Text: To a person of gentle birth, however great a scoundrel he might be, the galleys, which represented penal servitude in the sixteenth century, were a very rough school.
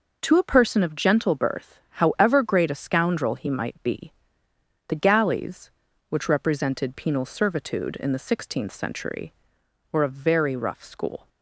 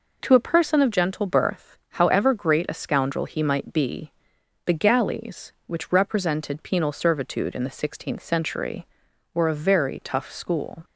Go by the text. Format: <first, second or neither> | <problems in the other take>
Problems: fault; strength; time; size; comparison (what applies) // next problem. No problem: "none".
first | says "tough" for "rough"; at 10.0 s